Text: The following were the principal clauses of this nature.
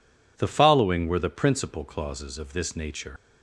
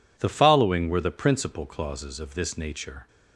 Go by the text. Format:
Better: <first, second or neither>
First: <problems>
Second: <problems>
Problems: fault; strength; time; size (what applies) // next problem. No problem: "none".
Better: second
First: leaves "nature" unfinished; at 3.1 s; 95 ms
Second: none